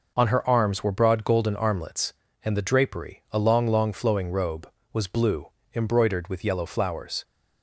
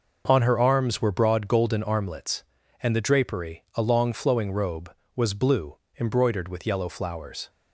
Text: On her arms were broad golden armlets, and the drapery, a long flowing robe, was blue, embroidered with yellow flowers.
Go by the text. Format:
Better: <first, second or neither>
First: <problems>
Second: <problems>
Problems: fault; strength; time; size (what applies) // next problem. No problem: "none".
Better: second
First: says "long" twice; at 3.6 s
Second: none